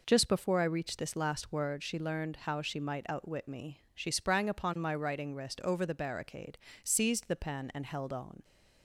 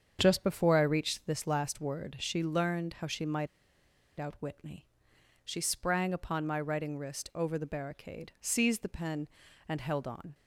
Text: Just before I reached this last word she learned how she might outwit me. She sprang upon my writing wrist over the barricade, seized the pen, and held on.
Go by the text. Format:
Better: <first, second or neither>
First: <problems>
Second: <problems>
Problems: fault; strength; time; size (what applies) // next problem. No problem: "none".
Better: first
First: none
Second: starts louder than the rest; strong; until 1.2 s; 7.5 dB // pauses between "might" and "outwit"; noticeable; at 3.4 s; 0.70 s long